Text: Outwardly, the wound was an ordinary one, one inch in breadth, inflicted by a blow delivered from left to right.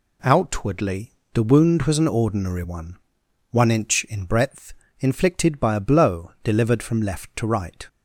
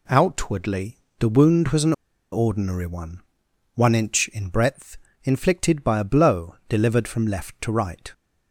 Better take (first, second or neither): first